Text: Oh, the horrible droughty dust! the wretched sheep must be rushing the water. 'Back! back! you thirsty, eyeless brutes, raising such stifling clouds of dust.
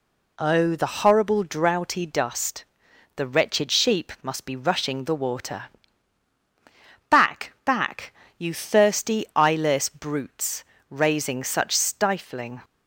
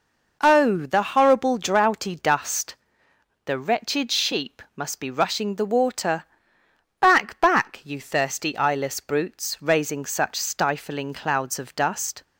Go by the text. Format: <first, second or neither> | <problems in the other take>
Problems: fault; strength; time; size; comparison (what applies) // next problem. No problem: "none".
second | stops before "clouds of dust"; at 12.6 s